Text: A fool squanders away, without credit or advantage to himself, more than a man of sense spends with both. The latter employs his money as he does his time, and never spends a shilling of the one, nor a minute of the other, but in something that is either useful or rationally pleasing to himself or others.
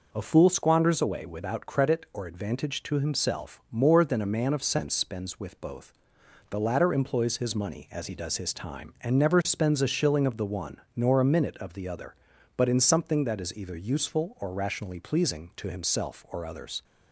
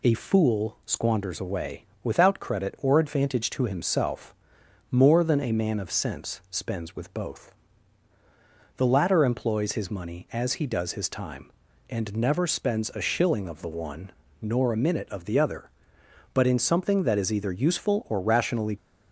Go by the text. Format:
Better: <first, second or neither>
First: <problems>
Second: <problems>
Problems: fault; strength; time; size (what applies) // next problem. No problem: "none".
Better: first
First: none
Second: stops before "pleasing to himself or others"; at 18.7 s